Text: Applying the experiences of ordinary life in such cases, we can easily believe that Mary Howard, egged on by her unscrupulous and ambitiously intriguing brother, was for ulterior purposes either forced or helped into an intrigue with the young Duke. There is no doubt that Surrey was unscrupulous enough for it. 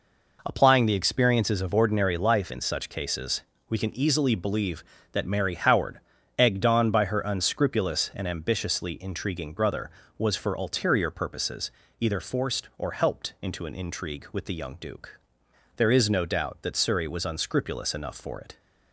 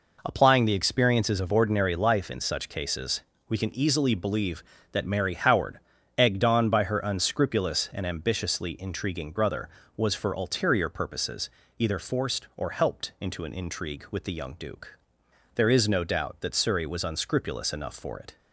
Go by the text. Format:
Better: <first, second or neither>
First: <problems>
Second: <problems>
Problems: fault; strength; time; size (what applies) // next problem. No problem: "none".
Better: neither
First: pauses between "purposes" and "either"; slight; at 11.7 s; 0.28 s long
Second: pauses between "purposes" and "either"; slight; at 11.4 s; 0.28 s long